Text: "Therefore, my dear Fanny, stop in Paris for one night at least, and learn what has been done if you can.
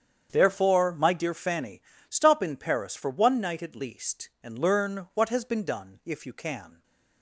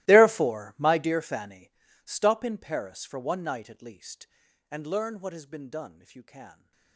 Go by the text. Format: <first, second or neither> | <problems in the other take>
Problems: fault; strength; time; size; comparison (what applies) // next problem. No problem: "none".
first | gets quieter; strong; throughout; 22.5 dB // starts louder than the rest; strong; until 1.1 s; 17 dB; strong in the first